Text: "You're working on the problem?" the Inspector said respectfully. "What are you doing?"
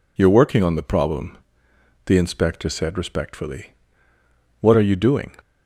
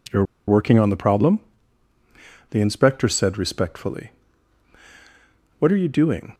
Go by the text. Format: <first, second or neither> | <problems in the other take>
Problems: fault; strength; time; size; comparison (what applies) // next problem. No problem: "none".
first | pauses between "You're" and "working"; slight; at 0.2 s; 0.24 s long